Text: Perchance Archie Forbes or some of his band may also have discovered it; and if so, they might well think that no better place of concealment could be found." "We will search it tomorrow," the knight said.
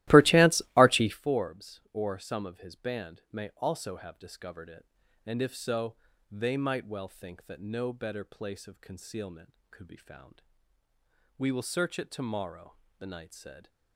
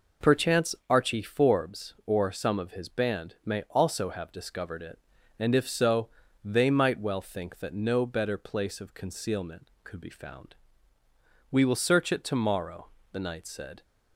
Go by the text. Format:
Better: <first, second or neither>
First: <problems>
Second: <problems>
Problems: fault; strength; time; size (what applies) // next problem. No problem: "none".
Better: second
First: starts louder than the rest; strong; until 1.2 s; 16.5 dB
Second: none